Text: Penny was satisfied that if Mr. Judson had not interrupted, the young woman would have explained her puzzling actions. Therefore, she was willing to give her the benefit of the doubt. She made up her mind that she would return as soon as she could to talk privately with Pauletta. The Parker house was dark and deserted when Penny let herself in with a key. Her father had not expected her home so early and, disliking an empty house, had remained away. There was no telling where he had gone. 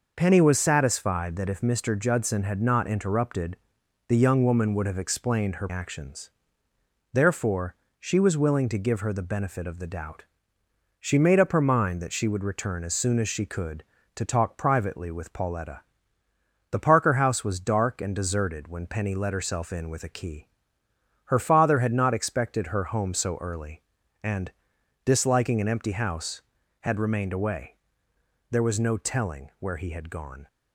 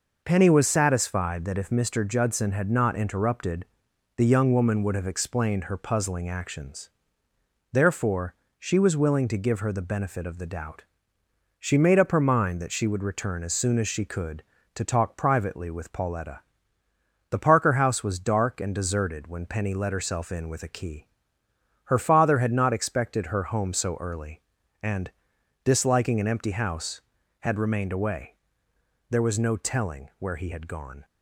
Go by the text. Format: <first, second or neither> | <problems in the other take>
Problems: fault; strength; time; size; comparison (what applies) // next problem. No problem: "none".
second | skips "puzzling"; at 5.6 s